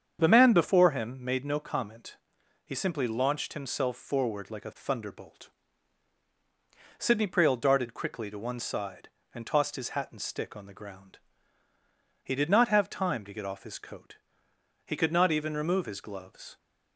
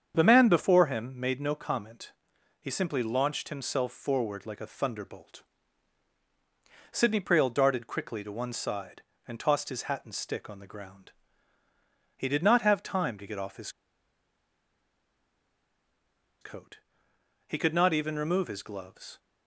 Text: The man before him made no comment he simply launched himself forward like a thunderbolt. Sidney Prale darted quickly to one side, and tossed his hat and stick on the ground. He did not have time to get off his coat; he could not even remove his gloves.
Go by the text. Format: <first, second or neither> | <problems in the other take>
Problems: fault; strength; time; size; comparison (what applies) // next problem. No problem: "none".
first | starts louder than the rest; strong; until 1.2 s; 7.5 dB; strong in the first // pauses between "comment" and "he"; noticeable; at 2.1 s; 0.48 s long; noticeable in the first // pauses between "his" and "coat"; strong; at 13.6 s; 2.7 s long